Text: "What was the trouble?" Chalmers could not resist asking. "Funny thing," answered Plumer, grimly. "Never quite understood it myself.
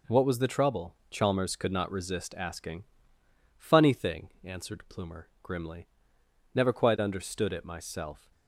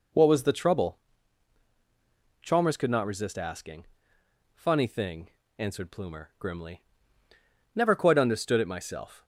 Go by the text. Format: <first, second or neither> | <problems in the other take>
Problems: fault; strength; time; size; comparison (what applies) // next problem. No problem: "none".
neither | none